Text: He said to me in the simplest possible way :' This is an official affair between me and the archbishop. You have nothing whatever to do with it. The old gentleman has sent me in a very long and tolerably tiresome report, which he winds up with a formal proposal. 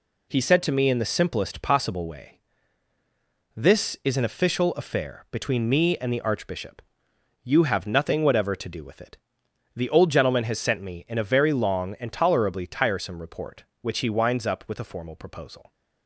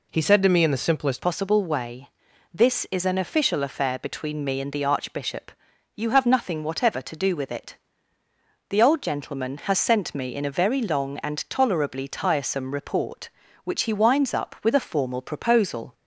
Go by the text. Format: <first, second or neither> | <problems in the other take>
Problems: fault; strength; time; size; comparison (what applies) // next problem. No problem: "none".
first | changes voice at "possible"; from 1.2 s on; 14.7 s long